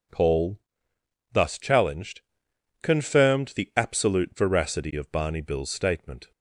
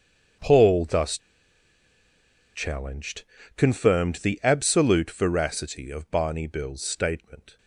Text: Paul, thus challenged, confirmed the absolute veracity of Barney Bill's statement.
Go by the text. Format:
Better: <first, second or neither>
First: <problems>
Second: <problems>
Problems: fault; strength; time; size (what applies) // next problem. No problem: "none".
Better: first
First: none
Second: starts louder than the rest; strong; until 2.7 s; 7.5 dB // pauses between "thus" and "challenged"; strong; at 1.1 s; 1.3 s long